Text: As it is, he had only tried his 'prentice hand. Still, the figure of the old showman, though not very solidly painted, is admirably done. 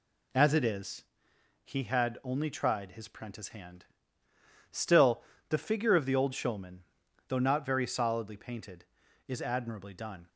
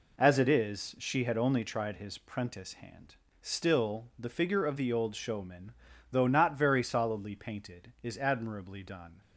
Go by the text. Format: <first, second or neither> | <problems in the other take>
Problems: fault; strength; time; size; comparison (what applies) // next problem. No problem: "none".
first | says "she" for "he"; at 0.9 s